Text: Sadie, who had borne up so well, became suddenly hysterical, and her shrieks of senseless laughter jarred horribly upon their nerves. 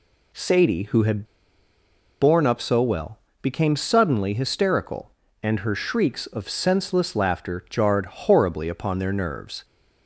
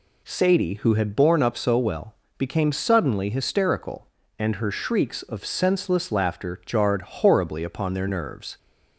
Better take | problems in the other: second | pauses between "had" and "borne"; at 1.2 s; 0.98 s long

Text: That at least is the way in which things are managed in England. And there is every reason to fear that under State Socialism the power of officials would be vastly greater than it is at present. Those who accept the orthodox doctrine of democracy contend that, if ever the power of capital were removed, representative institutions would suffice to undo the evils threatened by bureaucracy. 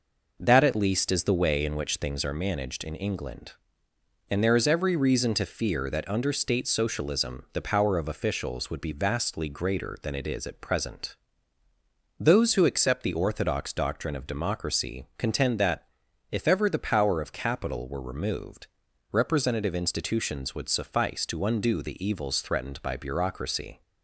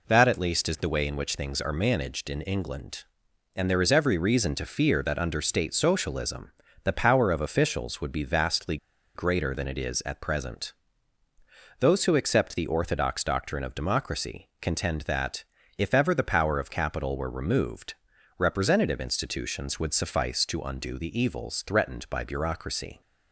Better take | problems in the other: first | pauses between "Socialism" and "the"; slight; at 6.5 s; 0.32 s long // pauses between "vastly" and "greater"; at 8.7 s; 0.38 s long

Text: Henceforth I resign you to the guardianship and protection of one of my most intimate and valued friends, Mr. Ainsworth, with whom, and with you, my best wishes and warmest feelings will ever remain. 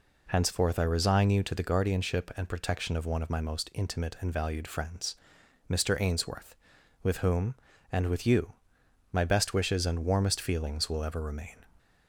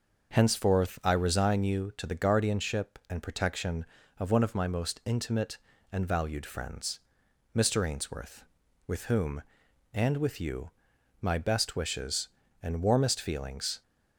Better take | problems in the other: first | starts louder than the rest; until 1.3 s; 6 dB // stops before "will ever remain"; at 13.8 s

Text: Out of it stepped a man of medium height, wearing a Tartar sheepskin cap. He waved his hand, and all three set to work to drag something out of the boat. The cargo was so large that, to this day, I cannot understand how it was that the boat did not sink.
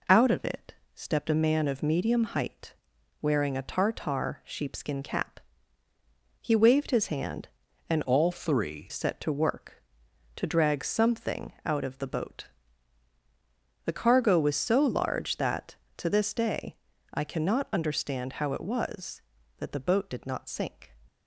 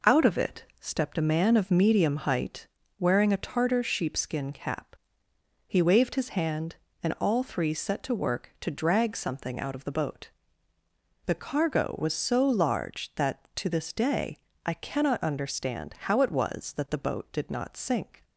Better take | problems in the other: second | pauses between "it" and "stepped"; slight; at 0.7 s; 0.20 s long; slight in the second // changes voice from "all" to "three"; from 8.0 to 8.8 s; 0.8 s long

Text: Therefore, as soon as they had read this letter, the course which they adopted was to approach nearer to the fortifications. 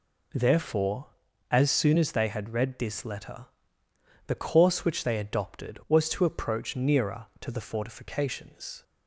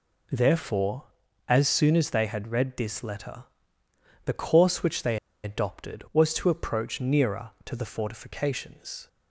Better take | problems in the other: first | pauses between "they" and "adopted"; slight; at 5.1 s; 0.27 s long

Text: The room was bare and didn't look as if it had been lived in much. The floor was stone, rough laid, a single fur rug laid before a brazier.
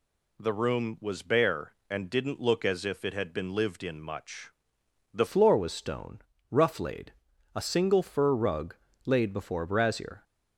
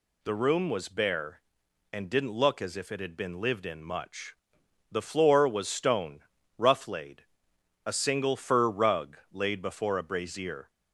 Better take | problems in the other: second | changes voice at "floor"; from 5.2 s on; 5.0 s long // pauses between "rug" and "laid"; slight; at 8.7 s; 0.30 s long; slight in the second

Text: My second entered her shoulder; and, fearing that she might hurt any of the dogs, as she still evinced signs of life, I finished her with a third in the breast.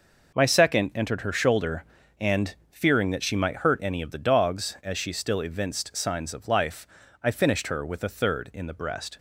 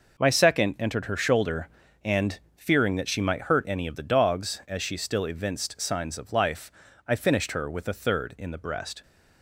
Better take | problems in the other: neither | none

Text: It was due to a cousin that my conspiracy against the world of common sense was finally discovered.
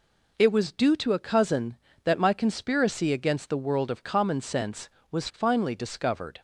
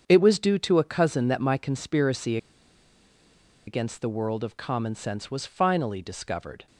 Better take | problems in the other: first | starts louder than the rest; strong; until 1.0 s; 7.5 dB // pauses between "conspiracy" and "against"; strong; at 2.3 s; 1.3 s long

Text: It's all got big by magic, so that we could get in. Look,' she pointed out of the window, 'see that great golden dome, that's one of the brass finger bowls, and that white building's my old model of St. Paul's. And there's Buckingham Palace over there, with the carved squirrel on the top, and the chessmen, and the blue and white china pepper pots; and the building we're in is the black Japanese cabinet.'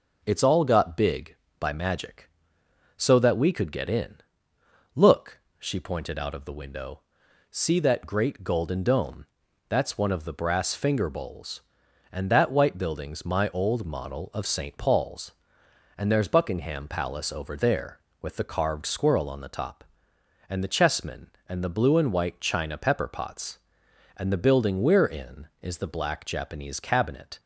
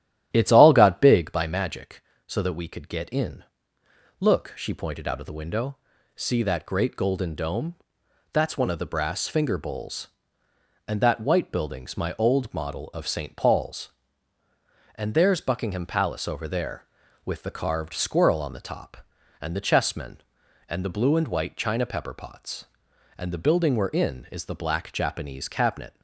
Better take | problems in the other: first | starts louder than the rest; strong; until 1.3 s; 11.5 dB

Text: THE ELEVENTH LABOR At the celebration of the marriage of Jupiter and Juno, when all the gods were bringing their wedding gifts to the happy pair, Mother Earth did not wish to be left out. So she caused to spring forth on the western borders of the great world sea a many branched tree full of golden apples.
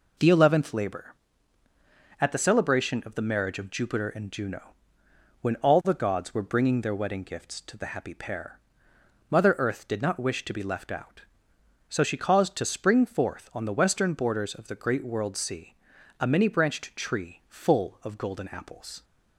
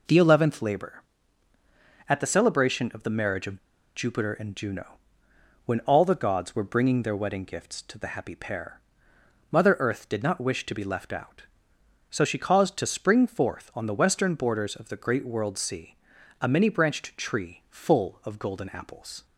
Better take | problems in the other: first | pauses between "of" and "Jupiter"; at 3.5 s; 0.38 s long // pauses between "sea" and "a"; noticeable; at 15.9 s; 0.46 s long; noticeable in the first

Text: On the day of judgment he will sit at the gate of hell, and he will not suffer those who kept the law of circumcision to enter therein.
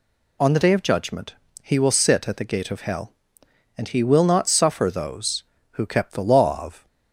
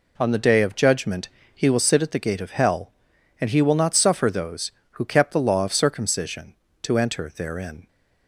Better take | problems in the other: second | pauses between "judgment" and "he"; slight; at 1.3 s; 0.26 s long; slight in the second // stops before "circumcision to enter therein"; at 6.8 s

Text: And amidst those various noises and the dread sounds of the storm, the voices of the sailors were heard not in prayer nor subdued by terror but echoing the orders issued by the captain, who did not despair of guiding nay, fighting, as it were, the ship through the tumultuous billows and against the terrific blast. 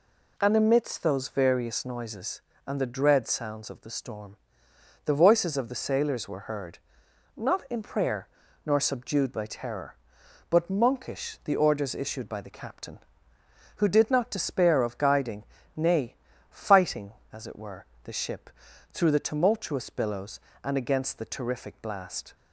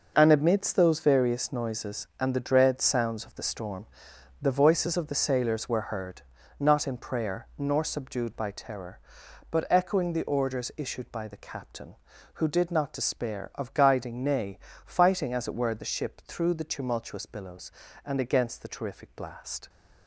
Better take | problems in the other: second | pauses between "heard" and "not"; noticeable; at 6.7 s; 0.58 s long; also in the second // pauses between "prayer" and "nor"; at 8.2 s; 0.38 s long // says "monkish" for "echoing"; at 10.7 s // pauses between "guiding" and "nay"; slight; at 15.4 s; 0.30 s long // pauses between "ship" and "through"; at 18.4 s; 0.42 s long

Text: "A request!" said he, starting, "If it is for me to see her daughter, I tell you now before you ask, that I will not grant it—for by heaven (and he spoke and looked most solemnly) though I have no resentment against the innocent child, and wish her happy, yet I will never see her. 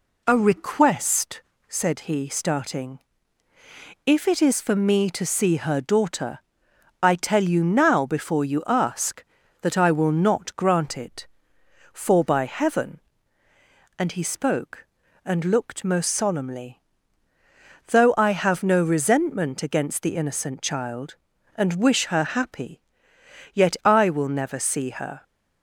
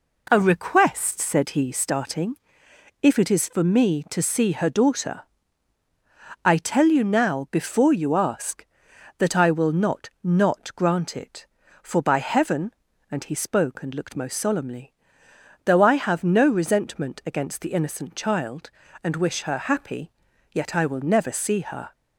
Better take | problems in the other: first | says "not" twice; at 10.2 s

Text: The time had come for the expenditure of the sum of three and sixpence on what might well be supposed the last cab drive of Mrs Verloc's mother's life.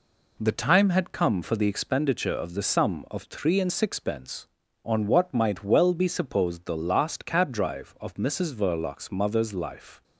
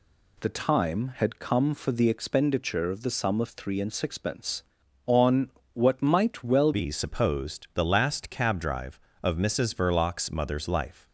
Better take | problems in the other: first | pauses between "on" and "what"; slight; at 5.5 s; 0.22 s long // changes voice at "be"; from 6.7 s on; 4.3 s long

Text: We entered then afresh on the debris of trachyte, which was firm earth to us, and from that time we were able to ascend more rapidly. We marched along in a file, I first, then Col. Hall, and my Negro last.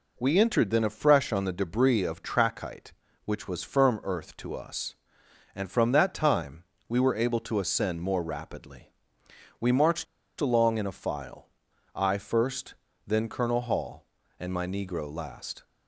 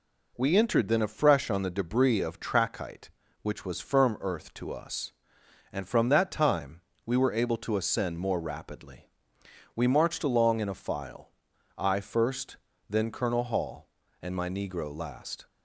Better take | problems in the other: second | pauses between "time" and "we"; slight; at 6.6 s; 0.24 s long; slight in the second // pauses between "marched" and "along"; slight; at 10.0 s; 0.35 s long

